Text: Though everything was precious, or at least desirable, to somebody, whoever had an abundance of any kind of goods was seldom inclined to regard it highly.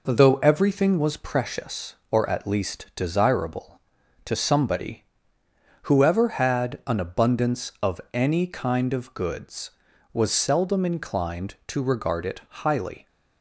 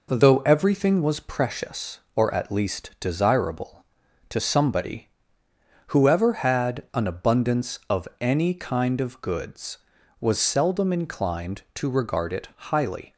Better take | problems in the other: neither | none

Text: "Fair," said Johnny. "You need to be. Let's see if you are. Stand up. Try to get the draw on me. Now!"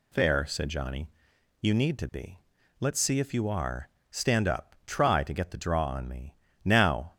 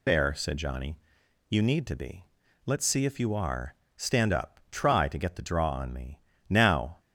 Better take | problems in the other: first | loses the start of "Fair"; at 0.0 s; 60 ms

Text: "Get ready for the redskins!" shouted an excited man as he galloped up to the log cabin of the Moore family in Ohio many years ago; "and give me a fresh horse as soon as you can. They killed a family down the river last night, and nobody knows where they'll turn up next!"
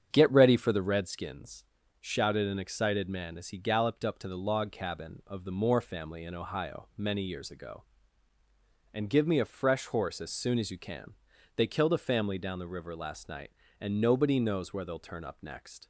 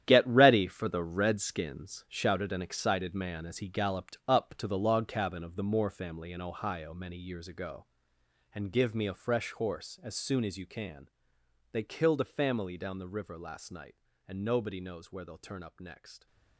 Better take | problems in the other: first | gets quieter; strong; throughout; 11 dB // starts louder than the rest; strong; until 1.0 s; 10.5 dB; strong in the first

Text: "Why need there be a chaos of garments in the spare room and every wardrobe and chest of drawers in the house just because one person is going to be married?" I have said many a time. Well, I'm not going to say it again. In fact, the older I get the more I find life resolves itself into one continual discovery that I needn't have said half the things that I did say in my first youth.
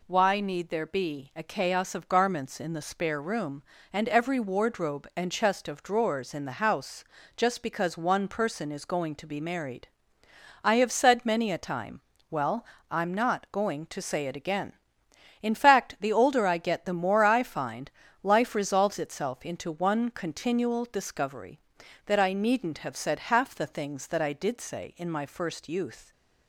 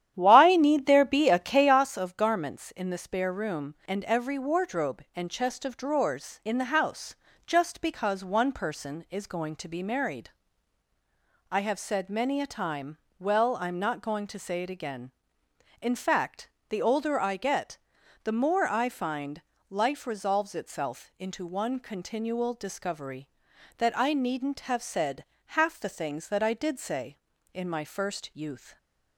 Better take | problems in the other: first | starts louder than the rest; strong; until 1.8 s; 10.5 dB // pauses between "house" and "just"; slight; at 7.1 s; 0.30 s long; slight in the first // pauses between "get" and "the"; noticeable; at 17.7 s; 0.46 s long // pauses between "find" and "life"; slight; at 19.4 s; 0.28 s long; slight in the first // pauses between "said" and "half"; slight; at 25.2 s; 0.22 s long

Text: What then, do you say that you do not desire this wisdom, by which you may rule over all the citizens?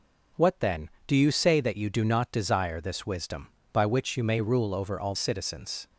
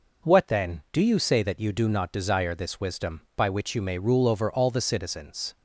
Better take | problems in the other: second | skips "the"; at 5.1 s

